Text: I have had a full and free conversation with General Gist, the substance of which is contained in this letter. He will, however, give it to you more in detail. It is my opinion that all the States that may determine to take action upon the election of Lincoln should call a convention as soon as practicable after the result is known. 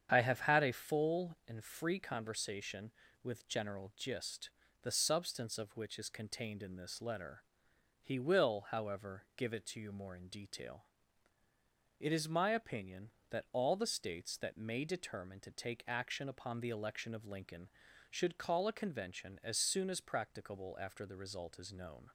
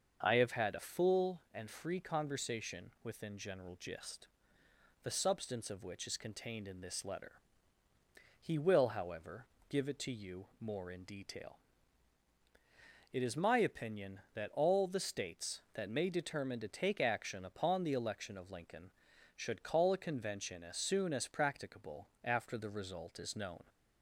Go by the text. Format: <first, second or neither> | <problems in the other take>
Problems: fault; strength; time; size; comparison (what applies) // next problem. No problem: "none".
first | starts louder than the rest; until 1.2 s; 6.5 dB; strong in the first // says "within" for "with"; at 3.0 s // pauses between "practicable" and "after"; slight; at 22.0 s; 0.16 s long